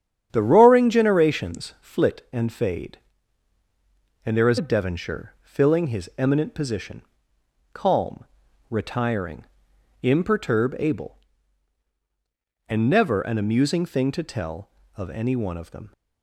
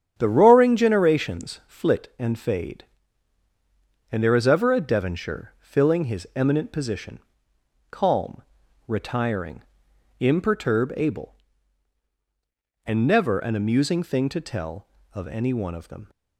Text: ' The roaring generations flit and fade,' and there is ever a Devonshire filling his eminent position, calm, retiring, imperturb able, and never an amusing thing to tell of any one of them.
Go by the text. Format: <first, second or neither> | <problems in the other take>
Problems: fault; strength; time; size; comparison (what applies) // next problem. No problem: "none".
second | starts louder than the rest; strong; until 1.3 s; 9 dB; strong in the second // skips "ever"; at 4.5 s